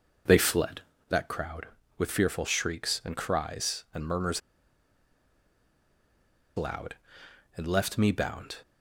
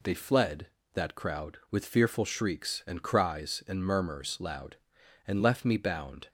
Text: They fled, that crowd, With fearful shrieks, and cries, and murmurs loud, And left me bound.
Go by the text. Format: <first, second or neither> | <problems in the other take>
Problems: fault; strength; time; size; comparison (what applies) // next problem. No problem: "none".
second | pauses between "murmurs" and "loud"; strong; at 4.4 s; 2.1 s long